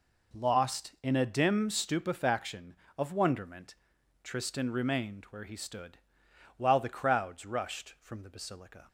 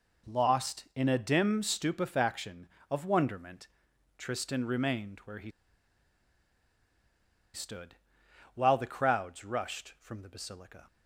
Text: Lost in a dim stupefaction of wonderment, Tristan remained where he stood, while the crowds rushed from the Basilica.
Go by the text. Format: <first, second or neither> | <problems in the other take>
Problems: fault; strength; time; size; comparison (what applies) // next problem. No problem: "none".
first | pauses between "he" and "stood"; strong; at 5.4 s; 2.0 s long